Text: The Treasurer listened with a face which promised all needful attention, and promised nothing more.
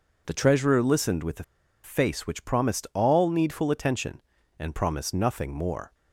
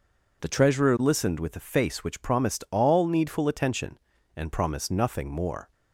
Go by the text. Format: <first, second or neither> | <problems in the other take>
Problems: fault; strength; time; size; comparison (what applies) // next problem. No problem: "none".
second | pauses between "a" and "face"; at 1.4 s; 0.41 s long